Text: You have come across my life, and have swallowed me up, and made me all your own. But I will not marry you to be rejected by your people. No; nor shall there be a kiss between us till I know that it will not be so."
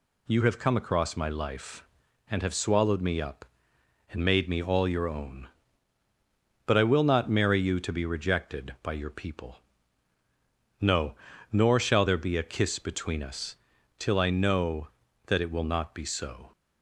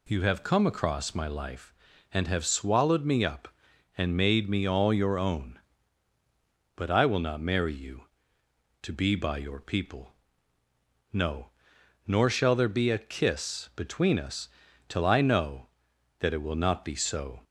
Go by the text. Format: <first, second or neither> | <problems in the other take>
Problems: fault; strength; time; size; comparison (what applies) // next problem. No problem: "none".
first | skips "rejected"; at 9.1 s // pauses between "us" and "till"; at 14.4 s; 0.40 s long; also in the first